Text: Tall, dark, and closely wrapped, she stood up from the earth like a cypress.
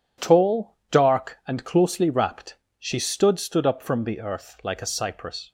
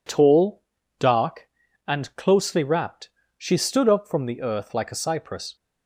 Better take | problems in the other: second | says "stood" twice; at 3.3 s

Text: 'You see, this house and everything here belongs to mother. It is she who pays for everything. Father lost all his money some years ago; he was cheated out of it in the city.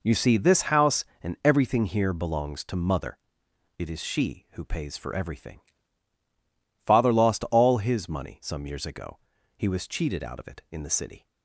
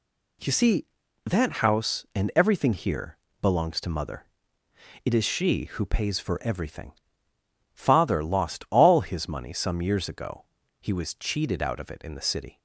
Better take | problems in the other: first | says "that" for "this"; at 1.2 s // pauses between "here" and "belongs"; slight; at 3.1 s; 0.24 s long

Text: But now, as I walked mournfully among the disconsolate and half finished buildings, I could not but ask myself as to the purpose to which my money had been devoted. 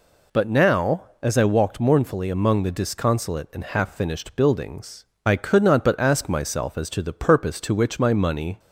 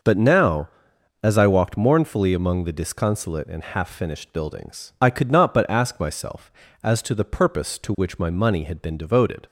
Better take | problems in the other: second | stops before "had been devoted"; at 8.5 s

